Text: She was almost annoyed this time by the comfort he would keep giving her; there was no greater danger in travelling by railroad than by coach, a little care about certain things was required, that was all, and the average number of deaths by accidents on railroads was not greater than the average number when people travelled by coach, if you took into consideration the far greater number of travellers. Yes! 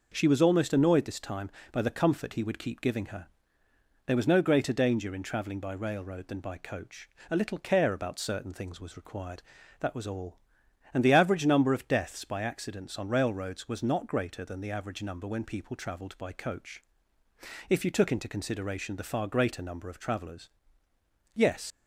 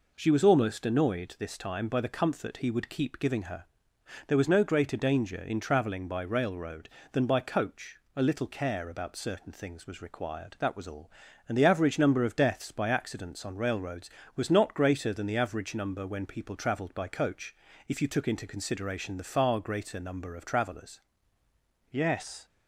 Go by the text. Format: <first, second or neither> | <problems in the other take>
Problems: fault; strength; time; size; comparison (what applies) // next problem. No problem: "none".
second | leaves "Yes" unfinished; at 21.7 s; 60 ms